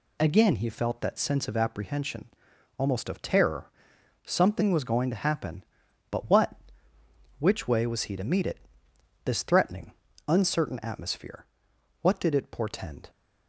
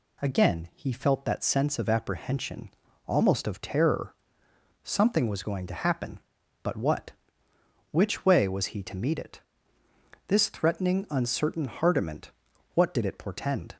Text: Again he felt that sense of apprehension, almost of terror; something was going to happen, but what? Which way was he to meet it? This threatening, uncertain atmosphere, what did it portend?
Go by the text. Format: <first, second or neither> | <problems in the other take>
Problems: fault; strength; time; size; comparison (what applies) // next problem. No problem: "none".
first | says "hardiment" for "atmosphere"; at 11.6 s